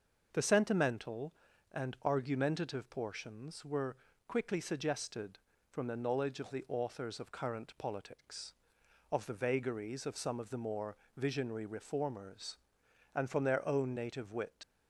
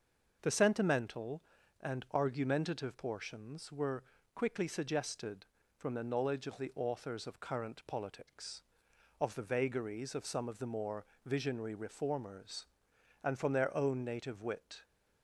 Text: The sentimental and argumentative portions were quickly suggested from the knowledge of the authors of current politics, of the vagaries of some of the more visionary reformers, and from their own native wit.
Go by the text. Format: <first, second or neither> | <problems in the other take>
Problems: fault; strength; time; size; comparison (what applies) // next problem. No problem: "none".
second | starts louder than the rest; until 1.3 s; 6.5 dB; also in the second // pauses between "were" and "quickly"; slight; at 3.9 s; 0.32 s long; slight in the second // pauses between "more" and "visionary"; slight; at 10.9 s; 0.20 s long; slight in the second // leaves "wit" unfinished; at 14.6 s; 100 ms